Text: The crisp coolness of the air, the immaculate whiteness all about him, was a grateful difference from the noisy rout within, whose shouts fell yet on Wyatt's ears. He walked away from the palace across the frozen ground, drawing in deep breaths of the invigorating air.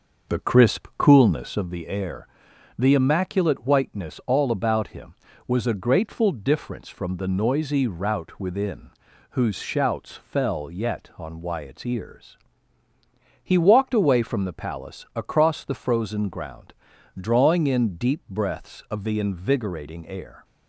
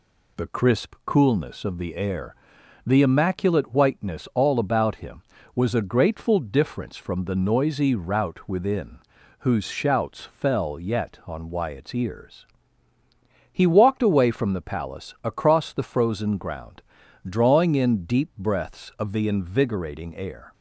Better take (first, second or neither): second